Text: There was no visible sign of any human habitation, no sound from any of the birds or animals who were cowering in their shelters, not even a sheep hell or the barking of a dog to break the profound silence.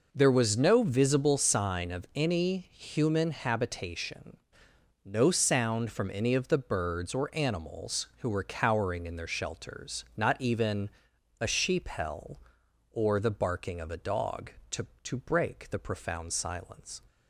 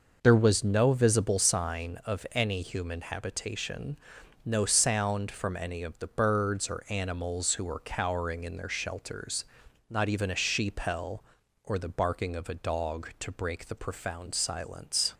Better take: second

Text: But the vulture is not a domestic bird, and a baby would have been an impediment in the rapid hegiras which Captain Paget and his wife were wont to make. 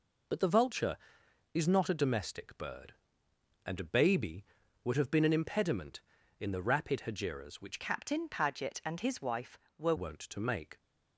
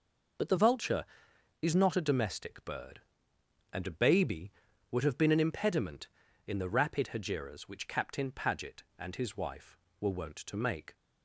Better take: second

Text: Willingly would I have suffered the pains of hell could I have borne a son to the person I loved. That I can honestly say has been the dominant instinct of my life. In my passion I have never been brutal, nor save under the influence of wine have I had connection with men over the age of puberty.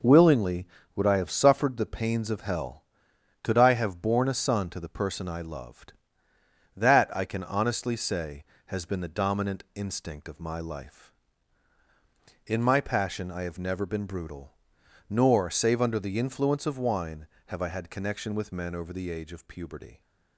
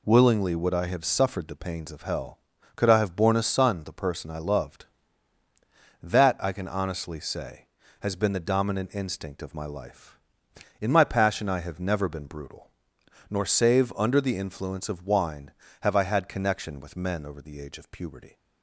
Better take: first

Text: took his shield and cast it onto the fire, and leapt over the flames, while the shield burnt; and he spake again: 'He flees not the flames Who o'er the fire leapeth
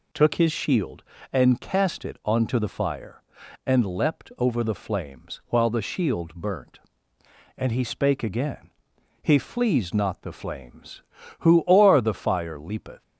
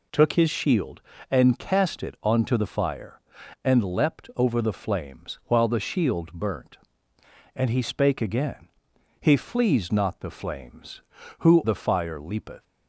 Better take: first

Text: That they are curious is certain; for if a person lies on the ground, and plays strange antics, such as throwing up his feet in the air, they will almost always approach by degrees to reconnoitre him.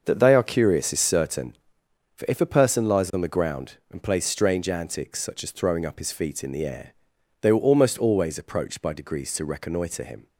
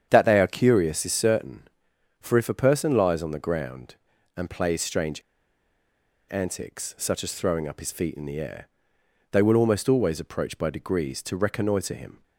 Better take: first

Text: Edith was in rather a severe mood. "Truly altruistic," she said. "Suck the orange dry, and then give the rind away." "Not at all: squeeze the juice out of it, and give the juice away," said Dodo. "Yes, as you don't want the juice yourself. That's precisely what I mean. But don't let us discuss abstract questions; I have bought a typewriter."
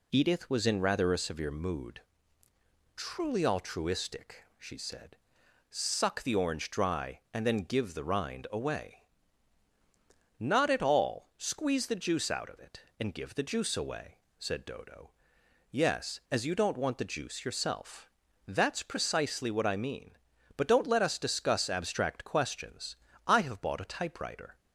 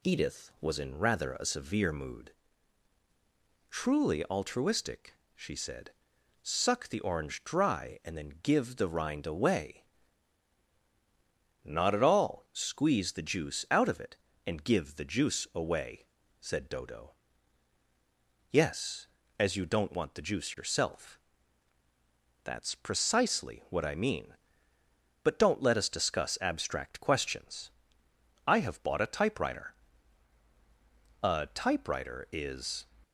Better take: first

